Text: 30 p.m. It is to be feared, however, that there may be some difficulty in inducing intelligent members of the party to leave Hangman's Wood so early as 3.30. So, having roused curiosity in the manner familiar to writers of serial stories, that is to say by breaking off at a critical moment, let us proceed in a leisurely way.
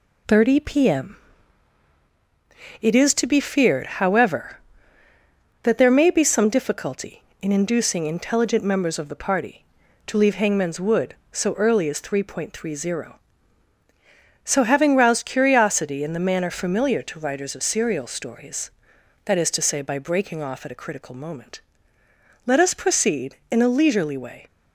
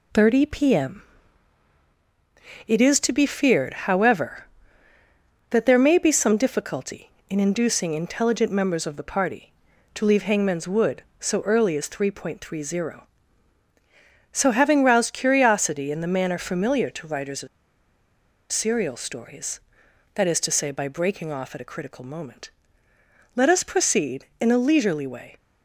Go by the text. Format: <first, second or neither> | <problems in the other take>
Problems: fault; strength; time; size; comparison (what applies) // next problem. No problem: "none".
first | pauses between "of" and "serial"; at 17.4 s; 1.0 s long